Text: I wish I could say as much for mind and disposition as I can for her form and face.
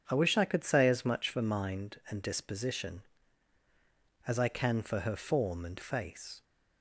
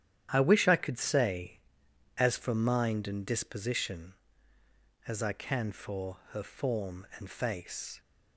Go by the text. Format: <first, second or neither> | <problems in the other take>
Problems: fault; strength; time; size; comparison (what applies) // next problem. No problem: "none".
first | starts louder than the rest; strong; until 1.3 s; 10.5 dB; strong in the first // skips "much"; at 2.3 s // pauses between "for" and "her"; slight; at 6.1 s; 0.16 s long